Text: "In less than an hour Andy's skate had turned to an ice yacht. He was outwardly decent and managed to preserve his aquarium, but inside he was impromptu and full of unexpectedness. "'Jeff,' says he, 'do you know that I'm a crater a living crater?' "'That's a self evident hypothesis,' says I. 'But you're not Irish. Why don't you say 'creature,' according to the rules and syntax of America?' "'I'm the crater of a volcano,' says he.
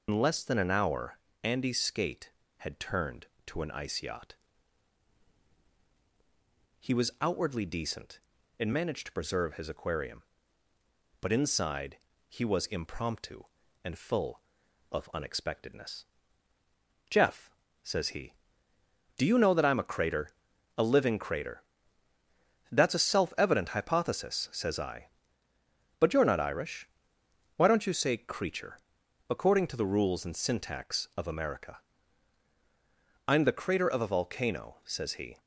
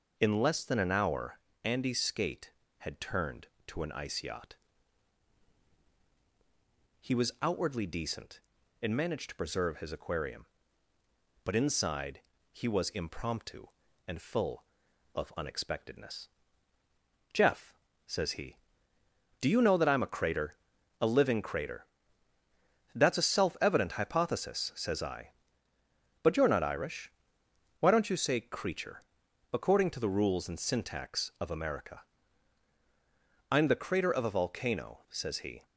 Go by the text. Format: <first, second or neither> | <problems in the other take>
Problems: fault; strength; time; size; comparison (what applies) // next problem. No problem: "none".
second | loses the start of "In"; at 0.0 s; 100 ms // pauses between "hour" and "Andy's"; slight; at 1.1 s; 0.24 s long; slight in the second // pauses between "inside" and "he"; slight; at 11.9 s; 0.30 s long; slight in the second // pauses between "crater" and "a"; noticeable; at 20.2 s; 0.48 s long; noticeable in the second